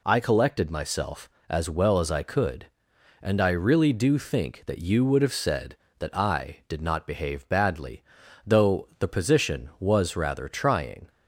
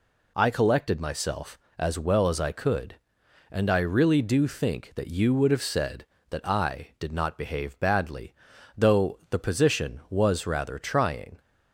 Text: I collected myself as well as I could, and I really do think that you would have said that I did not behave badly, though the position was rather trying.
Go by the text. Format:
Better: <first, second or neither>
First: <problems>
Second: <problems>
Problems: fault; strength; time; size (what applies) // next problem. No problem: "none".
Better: neither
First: none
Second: none